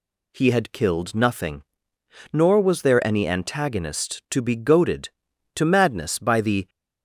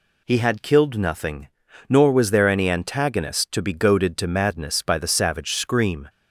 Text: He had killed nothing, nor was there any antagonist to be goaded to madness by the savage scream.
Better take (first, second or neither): second